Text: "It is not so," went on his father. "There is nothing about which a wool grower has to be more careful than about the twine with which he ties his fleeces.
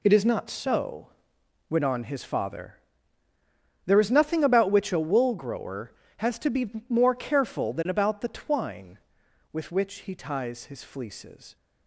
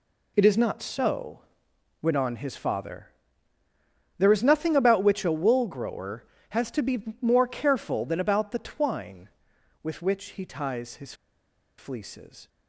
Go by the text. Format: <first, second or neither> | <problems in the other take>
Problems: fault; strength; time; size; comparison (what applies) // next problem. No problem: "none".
first | pauses between "his" and "fleeces"; noticeable; at 11.1 s; 0.64 s long